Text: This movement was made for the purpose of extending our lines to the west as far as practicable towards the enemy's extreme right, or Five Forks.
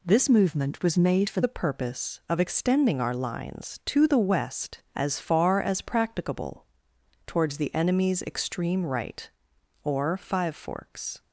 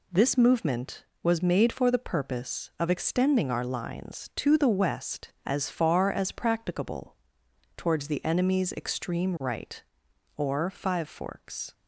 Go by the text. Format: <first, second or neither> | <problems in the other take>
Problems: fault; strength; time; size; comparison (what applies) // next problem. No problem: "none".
second | changes voice from "movement" to "for"; from 0.2 to 1.4 s; 1.2 s long // pauses between "practicable" and "towards"; noticeable; at 6.6 s; 0.60 s long; noticeable in the second